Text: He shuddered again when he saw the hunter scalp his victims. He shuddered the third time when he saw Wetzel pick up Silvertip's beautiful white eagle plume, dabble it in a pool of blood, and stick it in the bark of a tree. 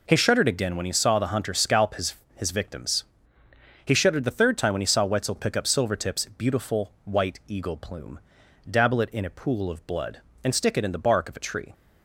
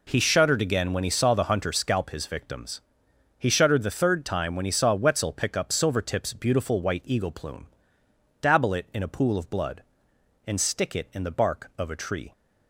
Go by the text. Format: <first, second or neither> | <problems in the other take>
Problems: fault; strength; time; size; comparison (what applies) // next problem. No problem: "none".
second | says "his" twice; at 2.3 s